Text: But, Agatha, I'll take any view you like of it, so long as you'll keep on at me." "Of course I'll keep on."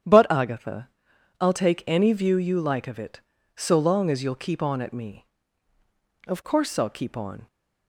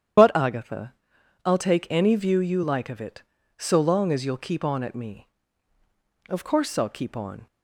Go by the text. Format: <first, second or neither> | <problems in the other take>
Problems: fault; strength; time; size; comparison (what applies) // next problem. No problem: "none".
first | loses the start of "But"; at 0.1 s; 85 ms // starts louder than the rest; strong; until 1.6 s; 9.5 dB; strong in the first